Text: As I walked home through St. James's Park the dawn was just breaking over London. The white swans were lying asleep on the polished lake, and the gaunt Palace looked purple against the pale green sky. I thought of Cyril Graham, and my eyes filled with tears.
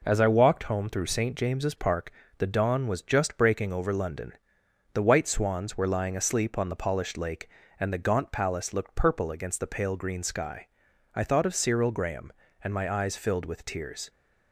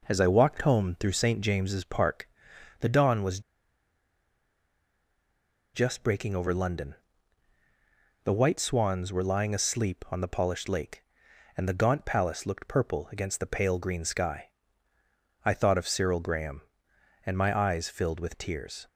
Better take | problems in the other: first | pauses between "Park" and "the"; noticeable; at 2.2 s; 0.54 s long; slight in the first // pauses between "was" and "just"; strong; at 3.3 s; 2.3 s long

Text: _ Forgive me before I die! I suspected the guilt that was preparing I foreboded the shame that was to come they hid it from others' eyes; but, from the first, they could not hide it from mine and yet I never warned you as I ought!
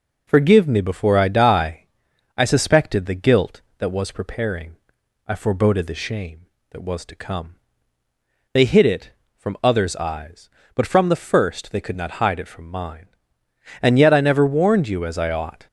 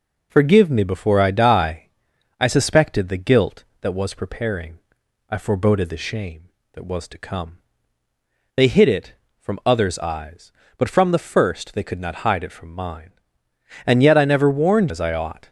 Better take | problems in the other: first | pauses between "preparing" and "I"; noticeable; at 4.7 s; 0.52 s long; noticeable in the first // pauses between "come" and "they"; noticeable; at 7.5 s; 0.98 s long; noticeable in the first // skips "you"; at 14.9 s

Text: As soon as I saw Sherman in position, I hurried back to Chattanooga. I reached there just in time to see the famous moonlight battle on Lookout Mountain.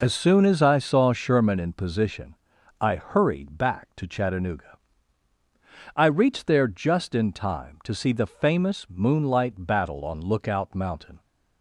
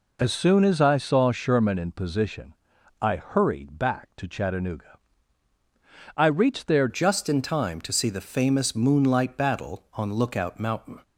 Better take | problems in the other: first | changes voice at "just"; from 6.8 s on; 4.2 s long

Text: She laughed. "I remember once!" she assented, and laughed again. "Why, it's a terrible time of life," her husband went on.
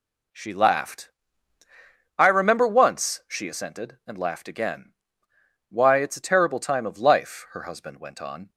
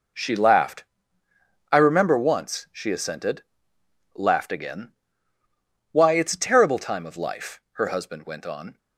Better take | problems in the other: first | skips "and"; at 3.7 s

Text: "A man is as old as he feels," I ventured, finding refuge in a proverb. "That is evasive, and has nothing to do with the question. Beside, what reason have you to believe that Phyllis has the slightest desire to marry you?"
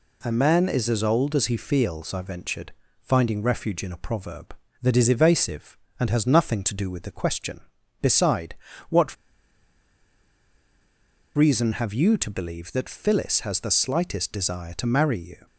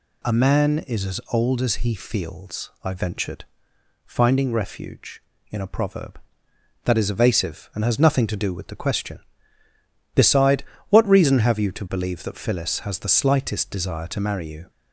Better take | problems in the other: second | pauses between "what" and "reason"; strong; at 9.1 s; 2.2 s long

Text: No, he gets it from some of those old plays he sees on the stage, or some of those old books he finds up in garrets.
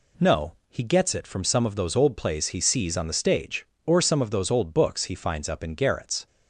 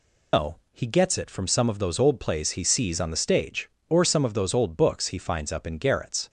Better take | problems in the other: first | loses the start of "No"; at 0.3 s; 150 ms

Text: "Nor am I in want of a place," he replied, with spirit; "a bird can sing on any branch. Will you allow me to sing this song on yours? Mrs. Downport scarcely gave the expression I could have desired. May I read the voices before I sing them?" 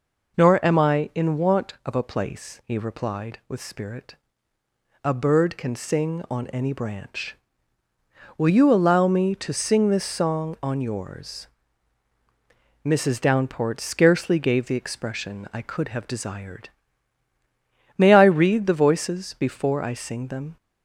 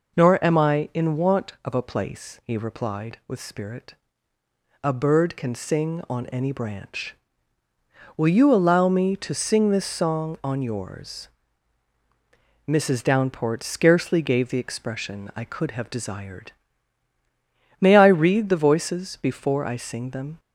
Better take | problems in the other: neither | none

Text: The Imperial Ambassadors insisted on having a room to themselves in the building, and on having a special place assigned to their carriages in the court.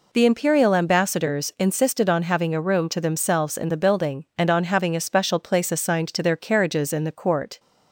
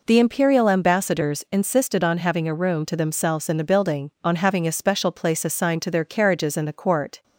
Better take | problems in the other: first | skips "and"; at 4.1 s

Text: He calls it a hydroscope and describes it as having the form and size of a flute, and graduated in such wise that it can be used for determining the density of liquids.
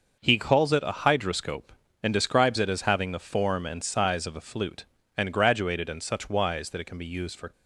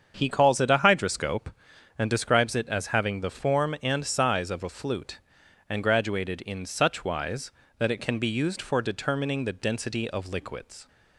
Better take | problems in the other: second | starts louder than the rest; noticeable; until 1.2 s; 6 dB; strong in the second // stops before "determining the density of liquids"; at 7.5 s

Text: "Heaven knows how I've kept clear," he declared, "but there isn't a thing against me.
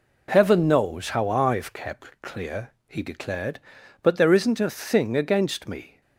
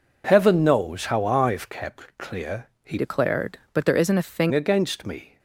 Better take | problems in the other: first | changes voice from "declared" to "thing"; from 2.9 to 4.5 s; 1.6 s long

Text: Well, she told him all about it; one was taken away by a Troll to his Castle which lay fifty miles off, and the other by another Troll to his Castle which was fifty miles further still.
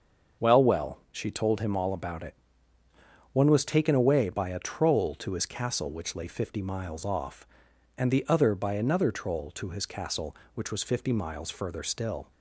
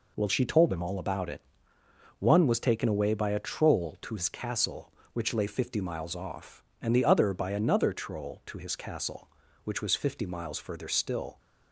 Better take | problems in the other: second | starts louder than the rest; until 1.5 s; 6.5 dB // says "Well" twice; at 0.6 s

